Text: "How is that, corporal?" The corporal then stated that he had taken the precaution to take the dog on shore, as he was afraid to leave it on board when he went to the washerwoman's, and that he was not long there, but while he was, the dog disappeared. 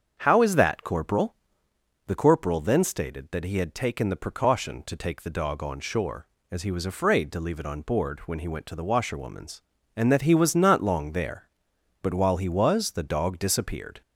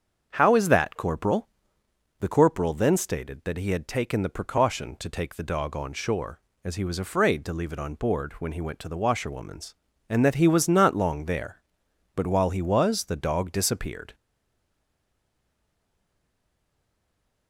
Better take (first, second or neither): first